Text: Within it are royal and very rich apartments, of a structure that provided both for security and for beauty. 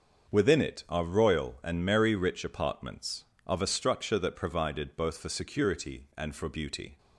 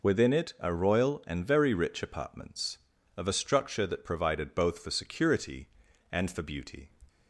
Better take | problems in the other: second | starts louder than the rest; until 1.3 s; 6.5 dB // says "merry" for "very"; at 1.8 s

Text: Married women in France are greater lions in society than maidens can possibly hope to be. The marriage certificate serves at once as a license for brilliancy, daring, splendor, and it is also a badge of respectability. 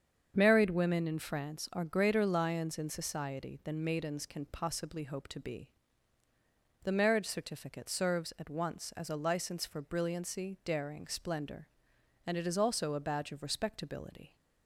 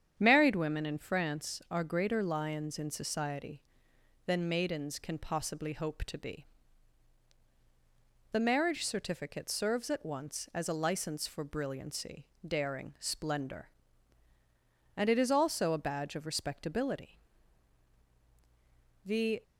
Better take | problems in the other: first | starts louder than the rest; strong; until 1.1 s; 8.5 dB; strong in the first // goes on to say "The"; slight; from 19.0 s on; 0.38 s long

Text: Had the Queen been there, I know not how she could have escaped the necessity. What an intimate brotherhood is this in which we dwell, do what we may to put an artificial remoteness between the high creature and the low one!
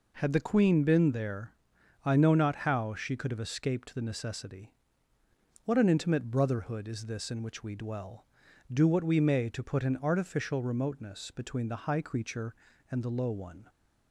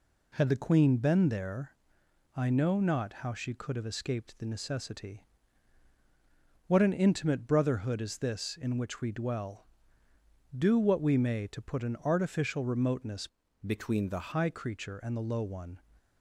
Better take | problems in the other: first | changes voice from "between" to "the"; from 13.6 to 14.1 s; 0.5 s long

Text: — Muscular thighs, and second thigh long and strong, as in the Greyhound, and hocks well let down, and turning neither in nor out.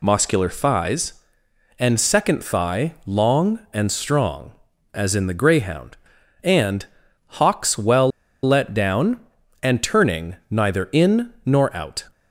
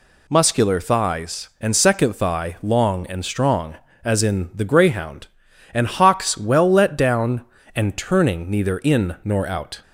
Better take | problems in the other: second | pauses between "and" and "hocks"; noticeable; at 6.8 s; 0.54 s long // pauses between "well" and "let"; slight; at 8.1 s; 0.35 s long

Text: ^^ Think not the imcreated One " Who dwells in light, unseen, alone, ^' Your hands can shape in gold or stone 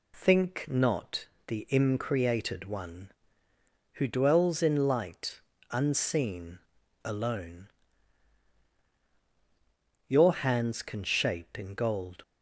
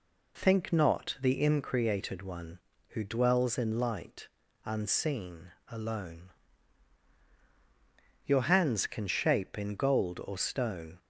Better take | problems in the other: second | pauses between "not" and "the"; slight; at 1.2 s; 0.22 s long // stops before "or stone"; at 12.2 s

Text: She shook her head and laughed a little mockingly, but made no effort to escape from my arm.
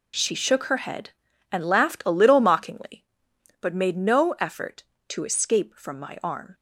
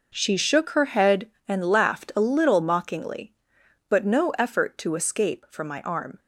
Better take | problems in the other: first | skips "made"; at 4.0 s

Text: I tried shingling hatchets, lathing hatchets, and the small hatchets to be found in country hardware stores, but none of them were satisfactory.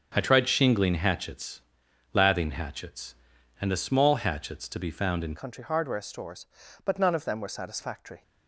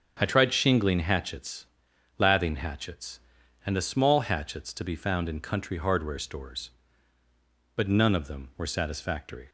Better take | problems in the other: second | starts louder than the rest; strong; until 1.1 s; 7 dB; strong in the second // changes voice at "country"; from 5.3 s on; 2.9 s long

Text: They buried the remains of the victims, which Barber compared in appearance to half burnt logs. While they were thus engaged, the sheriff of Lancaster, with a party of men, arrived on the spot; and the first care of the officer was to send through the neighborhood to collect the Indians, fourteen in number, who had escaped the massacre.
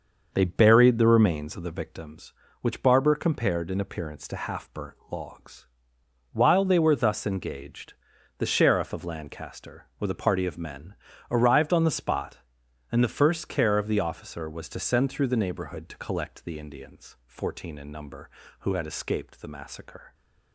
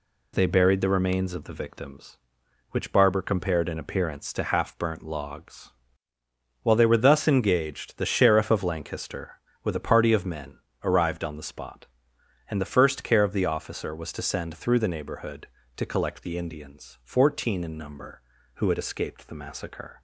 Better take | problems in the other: second | starts louder than the rest; until 2.0 s; 6 dB

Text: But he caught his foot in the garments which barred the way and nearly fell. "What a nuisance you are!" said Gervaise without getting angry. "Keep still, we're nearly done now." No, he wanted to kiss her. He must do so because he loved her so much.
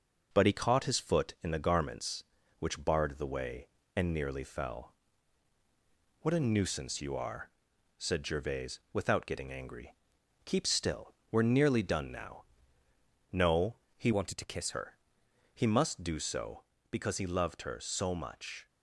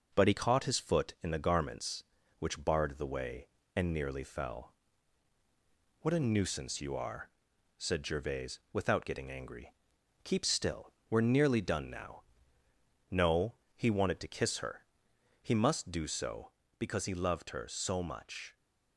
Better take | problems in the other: second | changes voice from "wanted" to "kiss"; from 14.1 to 14.7 s; 0.6 s long

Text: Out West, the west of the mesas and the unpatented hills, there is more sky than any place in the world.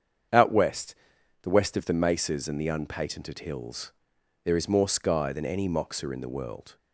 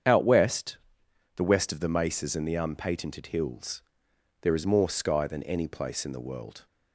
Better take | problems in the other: second | starts louder than the rest; strong; until 1.8 s; 7.5 dB; strong in the second // says "moxa" for "place"; at 5.6 s

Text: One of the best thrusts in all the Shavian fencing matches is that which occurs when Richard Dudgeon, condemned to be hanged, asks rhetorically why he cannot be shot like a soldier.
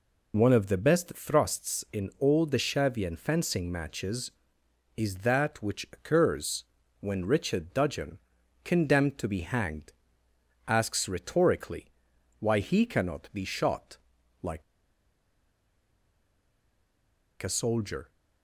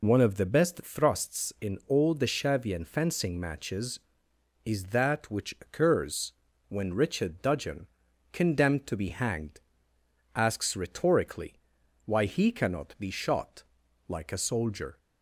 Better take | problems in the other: second | pauses between "occurs" and "when"; slight; at 6.6 s; 0.34 s long; slight in the second // pauses between "rhetorically" and "why"; noticeable; at 11.8 s; 0.54 s long; noticeable in the second // pauses between "shot" and "like"; noticeable; at 13.9 s; 0.46 s long; noticeable in the second // pauses between "like" and "a"; strong; at 14.6 s; 2.8 s long

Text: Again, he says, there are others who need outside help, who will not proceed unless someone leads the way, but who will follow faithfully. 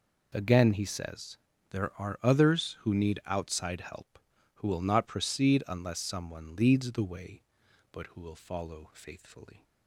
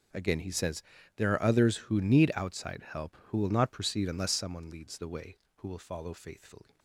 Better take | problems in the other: first | skips "but"; at 5.4 s

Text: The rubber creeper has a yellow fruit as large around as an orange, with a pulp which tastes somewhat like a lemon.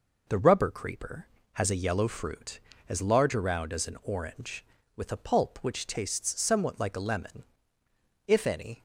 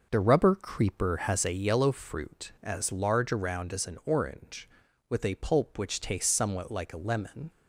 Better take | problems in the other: second | goes on to say "If any"; from 8.2 s on; 0.56 s long

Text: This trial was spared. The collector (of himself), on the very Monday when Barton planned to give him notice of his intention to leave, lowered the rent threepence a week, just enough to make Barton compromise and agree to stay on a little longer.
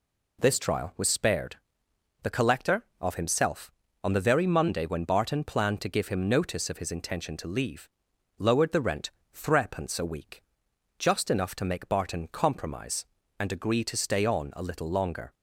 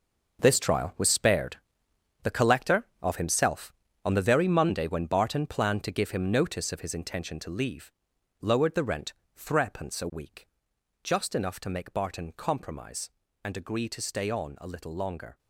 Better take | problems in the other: first | gets quieter; strong; throughout; 11 dB // pauses between "rent" and "threepence"; slight; at 9.1 s; 0.24 s long; slight in the first

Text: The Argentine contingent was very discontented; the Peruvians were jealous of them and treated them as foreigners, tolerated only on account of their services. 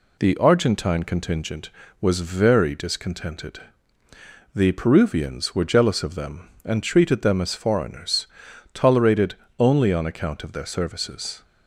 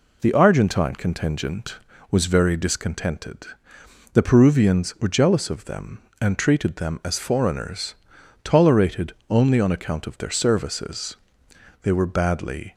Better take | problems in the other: first | pauses between "tolerated" and "only"; slight; at 9.1 s; 0.16 s long; slight in the first // goes on to say "They were badly"; noticeable; from 11.8 s on; 0.90 s long

